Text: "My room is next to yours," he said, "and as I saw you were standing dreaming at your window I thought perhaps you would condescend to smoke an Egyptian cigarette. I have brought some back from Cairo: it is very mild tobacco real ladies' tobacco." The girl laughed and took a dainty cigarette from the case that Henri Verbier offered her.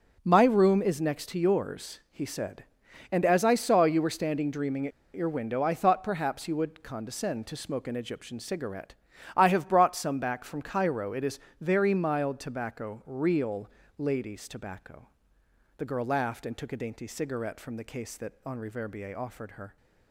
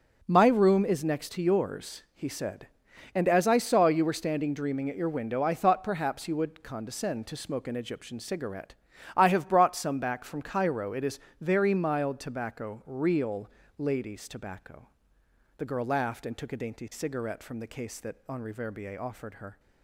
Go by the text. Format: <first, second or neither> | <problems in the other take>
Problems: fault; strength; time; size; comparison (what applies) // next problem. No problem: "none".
second | pauses between "at" and "your"; slight; at 4.9 s; 0.23 s long // pauses between "is" and "very"; slight; at 11.3 s; 0.22 s long; slight in the second // pauses between "real" and "ladies"; slight; at 13.7 s; 0.28 s long; slight in the second